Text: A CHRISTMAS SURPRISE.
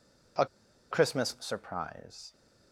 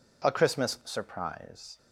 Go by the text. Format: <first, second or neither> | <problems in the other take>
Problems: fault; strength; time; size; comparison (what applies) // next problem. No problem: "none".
second | pauses between "A" and "CHRISTMAS"; noticeable; at 0.4 s; 0.46 s long